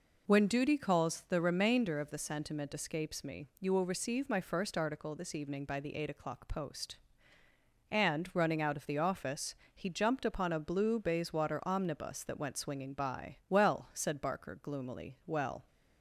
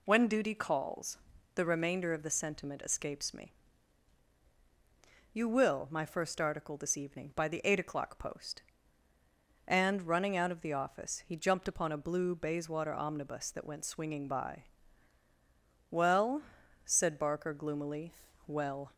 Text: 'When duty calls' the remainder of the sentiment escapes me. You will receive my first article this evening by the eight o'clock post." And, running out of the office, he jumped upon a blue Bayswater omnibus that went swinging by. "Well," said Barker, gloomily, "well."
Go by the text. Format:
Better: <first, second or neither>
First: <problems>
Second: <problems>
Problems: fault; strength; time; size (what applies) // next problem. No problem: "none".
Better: first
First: none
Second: pauses between "calls" and "the"; at 1.1 s; 0.38 s long // skips "receive"; at 5.8 s